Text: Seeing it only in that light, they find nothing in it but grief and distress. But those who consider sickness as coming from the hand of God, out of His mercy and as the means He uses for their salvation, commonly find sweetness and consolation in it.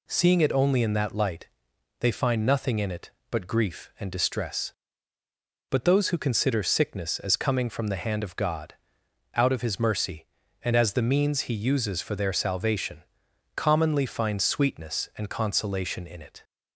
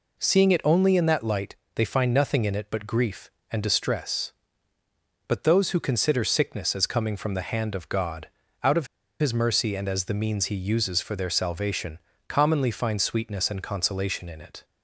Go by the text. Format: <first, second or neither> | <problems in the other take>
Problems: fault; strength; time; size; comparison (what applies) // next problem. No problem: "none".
first | pauses between "of" and "His"; slight; at 8.8 s; 0.35 s long